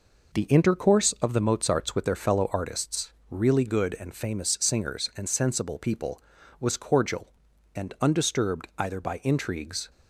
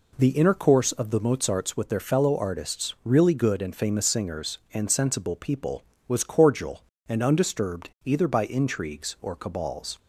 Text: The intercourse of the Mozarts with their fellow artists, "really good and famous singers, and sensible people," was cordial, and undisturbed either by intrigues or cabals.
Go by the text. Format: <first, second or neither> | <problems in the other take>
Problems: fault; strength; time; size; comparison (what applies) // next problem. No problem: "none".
second | stops before "or cabals"; at 9.8 s